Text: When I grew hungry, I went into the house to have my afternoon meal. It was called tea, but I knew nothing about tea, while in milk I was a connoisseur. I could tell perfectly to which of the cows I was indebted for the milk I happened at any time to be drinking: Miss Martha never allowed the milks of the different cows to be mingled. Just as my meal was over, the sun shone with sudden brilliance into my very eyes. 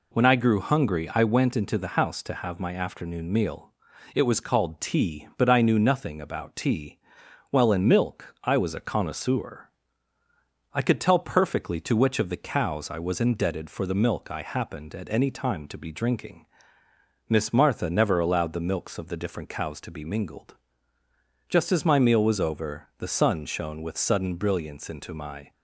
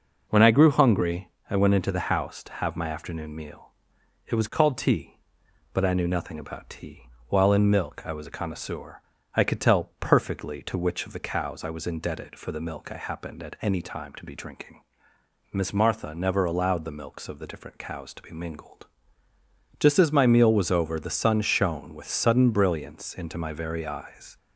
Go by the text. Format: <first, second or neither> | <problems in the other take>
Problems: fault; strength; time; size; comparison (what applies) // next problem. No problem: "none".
second | stops before "very eyes"; at 25.5 s